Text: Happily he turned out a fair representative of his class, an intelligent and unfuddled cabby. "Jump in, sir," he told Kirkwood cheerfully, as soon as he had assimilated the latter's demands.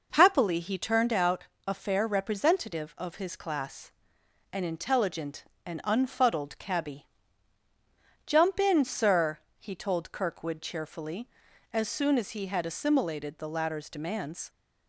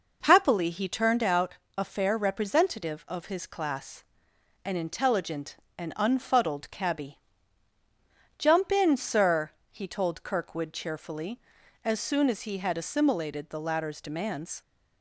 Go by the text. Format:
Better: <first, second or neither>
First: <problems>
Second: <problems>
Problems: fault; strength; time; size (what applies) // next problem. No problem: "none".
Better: neither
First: pauses between "out" and "a"; slight; at 1.4 s; 0.20 s long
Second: pauses between "out" and "a"; slight; at 1.5 s; 0.20 s long